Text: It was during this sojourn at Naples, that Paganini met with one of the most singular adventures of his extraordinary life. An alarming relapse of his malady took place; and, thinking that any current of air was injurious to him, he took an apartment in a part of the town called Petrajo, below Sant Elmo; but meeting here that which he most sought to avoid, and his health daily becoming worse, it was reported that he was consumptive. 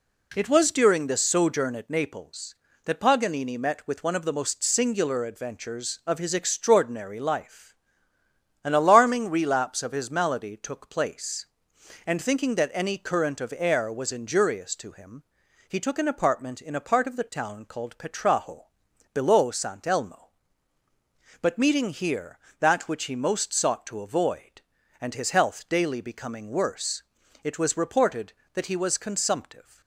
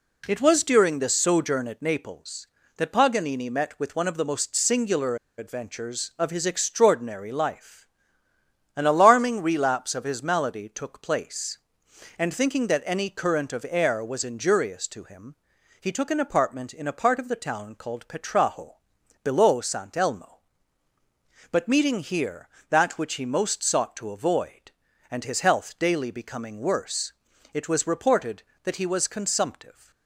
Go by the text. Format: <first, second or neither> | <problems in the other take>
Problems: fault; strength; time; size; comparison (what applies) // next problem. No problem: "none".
first | pauses between "singular" and "adventures"; slight; at 5.1 s; 0.21 s long